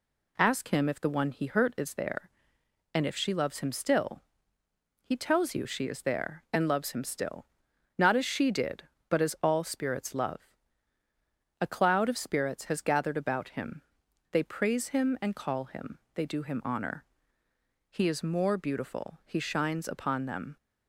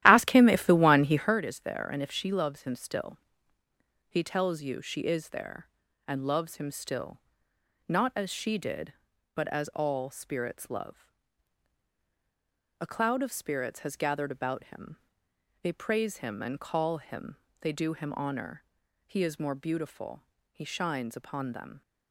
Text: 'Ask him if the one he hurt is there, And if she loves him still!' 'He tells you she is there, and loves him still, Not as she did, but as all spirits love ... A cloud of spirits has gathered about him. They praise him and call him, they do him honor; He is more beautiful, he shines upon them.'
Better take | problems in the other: first | starts louder than the rest; strong; until 1.3 s; 13 dB

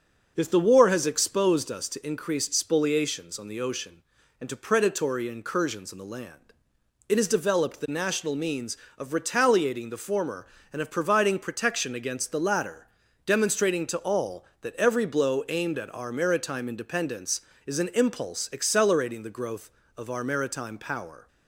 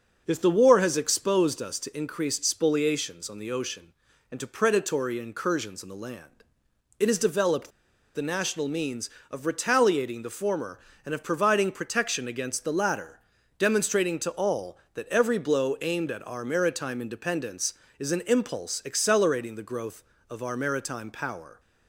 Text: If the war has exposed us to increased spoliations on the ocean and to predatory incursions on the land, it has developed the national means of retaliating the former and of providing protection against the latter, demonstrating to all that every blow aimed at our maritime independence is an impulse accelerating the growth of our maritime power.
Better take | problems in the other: first | starts louder than the rest; noticeable; until 1.2 s; 6 dB; noticeable in the first // pauses between "developed" and "the"; at 7.6 s; 0.45 s long

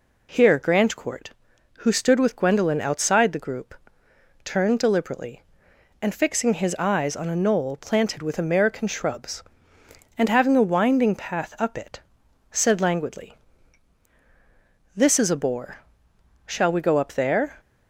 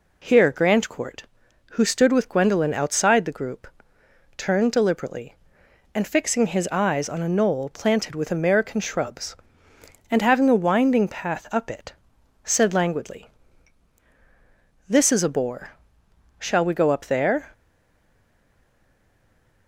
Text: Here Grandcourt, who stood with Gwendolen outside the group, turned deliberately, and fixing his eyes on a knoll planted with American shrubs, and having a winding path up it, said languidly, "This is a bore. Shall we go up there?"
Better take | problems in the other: first | stays silent after the last word; from 17.5 s on; 2.1 s long

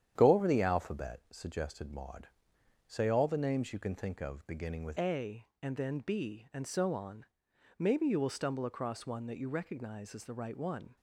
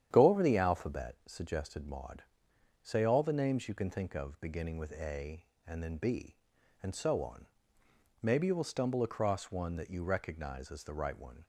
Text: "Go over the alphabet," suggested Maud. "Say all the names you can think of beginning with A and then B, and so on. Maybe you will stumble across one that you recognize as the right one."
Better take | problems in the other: second | starts louder than the rest; strong; until 1.1 s; 9.5 dB; strong in the second // changes voice at "A"; from 4.9 s on; 6.0 s long

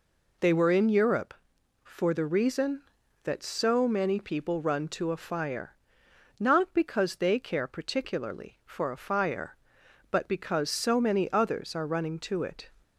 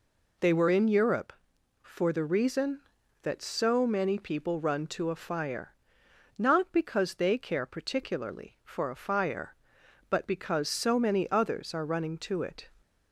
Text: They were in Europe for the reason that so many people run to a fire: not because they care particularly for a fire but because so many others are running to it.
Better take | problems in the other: neither | none

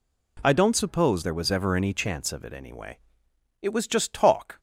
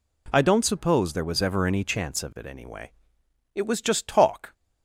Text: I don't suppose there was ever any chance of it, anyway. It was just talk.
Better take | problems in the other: neither | none

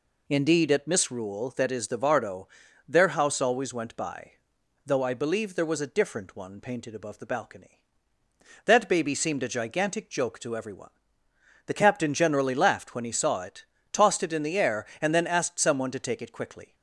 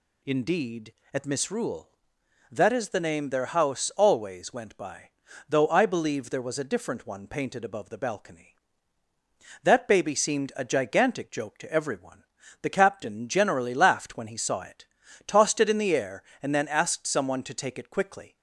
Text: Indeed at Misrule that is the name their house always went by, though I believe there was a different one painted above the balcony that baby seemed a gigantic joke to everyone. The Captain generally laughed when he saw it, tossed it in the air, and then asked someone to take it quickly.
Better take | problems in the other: second | says "vardo" for "name"; at 1.9 s

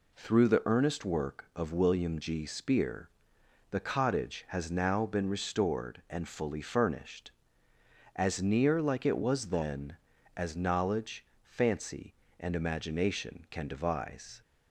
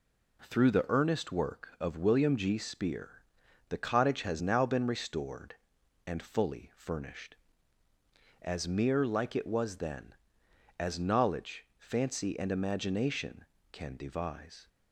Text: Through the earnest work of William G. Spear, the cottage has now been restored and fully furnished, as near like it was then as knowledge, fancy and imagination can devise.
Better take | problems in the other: first | says "mere" for "near"; at 8.6 s

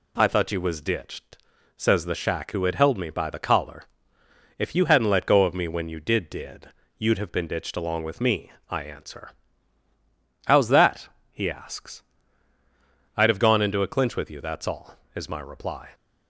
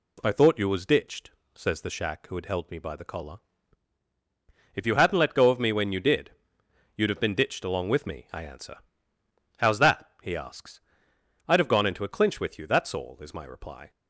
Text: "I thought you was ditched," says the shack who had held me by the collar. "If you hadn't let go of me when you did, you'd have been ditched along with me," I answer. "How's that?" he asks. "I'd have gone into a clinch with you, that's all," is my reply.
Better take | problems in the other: second | says "did" twice; at 6.3 s

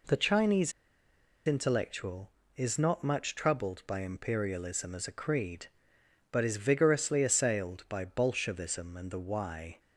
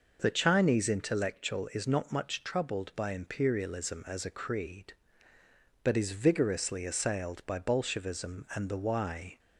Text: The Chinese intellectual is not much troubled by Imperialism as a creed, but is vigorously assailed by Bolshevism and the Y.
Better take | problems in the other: second | pauses between "Chinese" and "intellectual"; noticeable; at 0.7 s; 0.74 s long

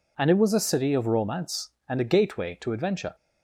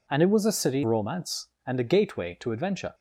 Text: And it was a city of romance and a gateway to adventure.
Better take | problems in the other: first | skips "of"; at 0.8 s

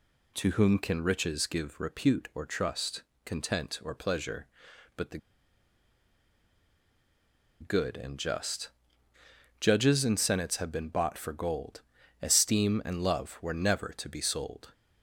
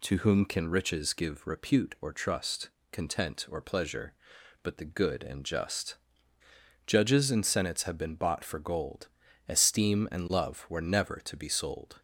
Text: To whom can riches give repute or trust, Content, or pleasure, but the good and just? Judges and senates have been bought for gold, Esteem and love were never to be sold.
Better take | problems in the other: second | pauses between "the" and "good"; strong; at 5.1 s; 2.4 s long

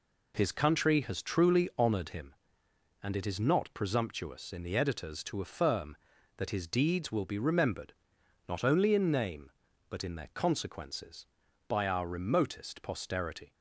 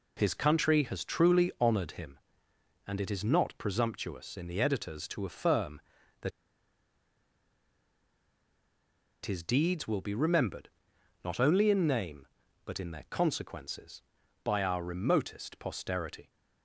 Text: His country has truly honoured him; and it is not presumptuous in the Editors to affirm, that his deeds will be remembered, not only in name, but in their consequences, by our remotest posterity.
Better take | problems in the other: first | pauses between "that" and "his"; strong; at 6.3 s; 2.9 s long

